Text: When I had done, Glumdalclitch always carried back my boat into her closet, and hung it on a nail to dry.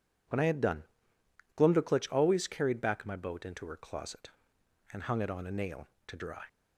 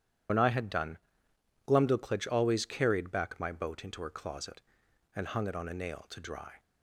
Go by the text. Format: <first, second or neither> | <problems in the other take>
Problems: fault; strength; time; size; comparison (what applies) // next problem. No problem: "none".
first | loses the start of "When"; at 0.2 s; 65 ms